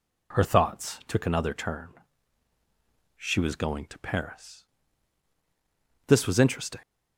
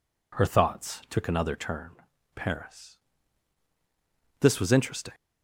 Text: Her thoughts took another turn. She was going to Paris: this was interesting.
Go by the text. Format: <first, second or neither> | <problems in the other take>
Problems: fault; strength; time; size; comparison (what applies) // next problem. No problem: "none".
first | skips "She was going to"; at 2.1 s